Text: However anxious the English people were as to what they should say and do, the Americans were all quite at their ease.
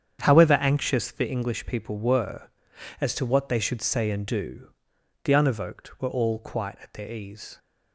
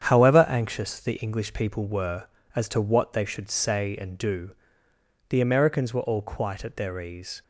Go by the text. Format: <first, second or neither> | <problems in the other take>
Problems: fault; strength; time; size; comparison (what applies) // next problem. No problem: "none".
second | starts louder than the rest; strong; until 1.2 s; 8 dB; strong in the second // says "Unevoked" for "Americans"; at 5.3 s